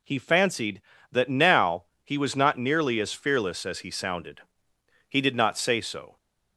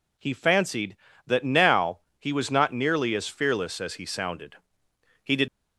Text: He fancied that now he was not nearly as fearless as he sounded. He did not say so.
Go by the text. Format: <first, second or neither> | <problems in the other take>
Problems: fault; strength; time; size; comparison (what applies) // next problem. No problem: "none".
first | pauses between "now" and "he"; slight; at 1.9 s; 0.20 s long; slight in the first // stops before "not say so"; at 5.4 s